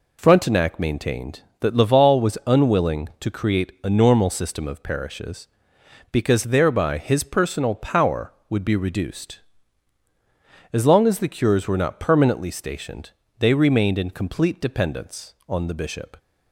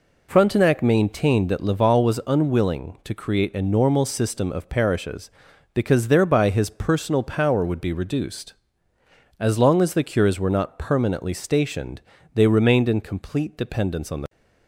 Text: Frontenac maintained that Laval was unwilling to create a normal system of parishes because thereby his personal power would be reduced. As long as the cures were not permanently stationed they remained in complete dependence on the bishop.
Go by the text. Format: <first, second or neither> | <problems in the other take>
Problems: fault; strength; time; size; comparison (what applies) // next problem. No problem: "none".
first | pauses between "stationed" and "they"; slight; at 11.9 s; 0.36 s long; slight in the first // stops before "bishop"; at 14.2 s